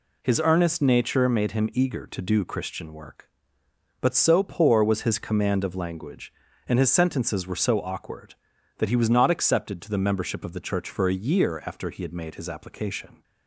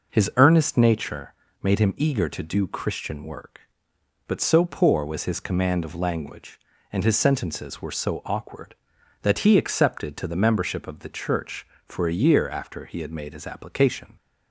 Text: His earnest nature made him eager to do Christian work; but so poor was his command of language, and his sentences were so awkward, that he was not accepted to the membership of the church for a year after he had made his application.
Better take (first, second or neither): first